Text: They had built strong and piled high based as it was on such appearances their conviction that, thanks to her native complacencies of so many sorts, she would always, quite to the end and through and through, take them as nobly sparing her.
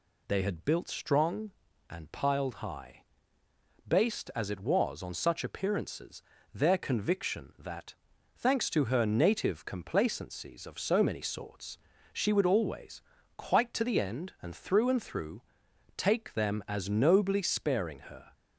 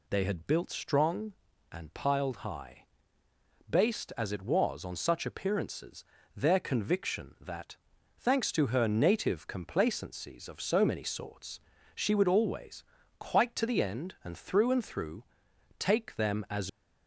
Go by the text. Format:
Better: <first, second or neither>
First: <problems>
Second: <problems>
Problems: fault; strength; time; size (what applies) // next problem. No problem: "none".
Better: first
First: pauses between "high" and "based"; noticeable; at 3.0 s; 0.84 s long // pauses between "appearances" and "their"; slight; at 6.2 s; 0.32 s long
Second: pauses between "high" and "based"; noticeable; at 2.8 s; 0.84 s long // pauses between "appearances" and "their"; slight; at 6.0 s; 0.32 s long // stops before "nobly sparing her"; at 16.6 s